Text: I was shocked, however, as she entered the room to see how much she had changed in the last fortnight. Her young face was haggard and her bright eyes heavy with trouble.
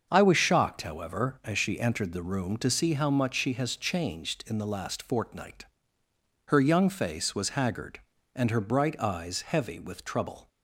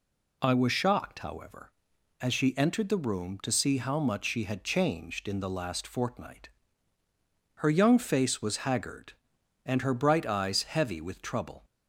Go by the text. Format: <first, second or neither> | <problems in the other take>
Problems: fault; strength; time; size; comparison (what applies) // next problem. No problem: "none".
second | starts louder than the rest; until 1.1 s; 6.5 dB // says "has" for "had"; at 3.5 s